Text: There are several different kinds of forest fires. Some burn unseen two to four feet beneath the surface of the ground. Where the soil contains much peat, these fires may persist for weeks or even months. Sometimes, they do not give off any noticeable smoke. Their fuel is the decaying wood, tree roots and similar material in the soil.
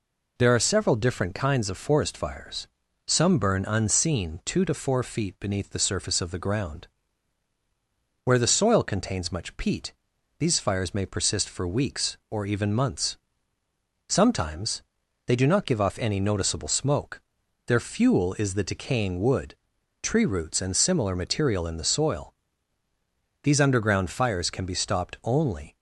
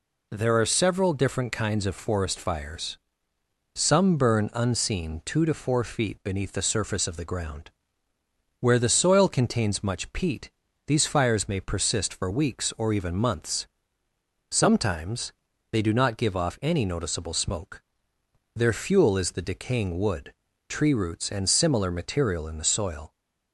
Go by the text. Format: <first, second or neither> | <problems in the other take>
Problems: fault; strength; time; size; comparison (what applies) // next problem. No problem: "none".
second | goes on to say "These underground fires can be stopped only"; strong; from 23.4 s on; 2.3 s long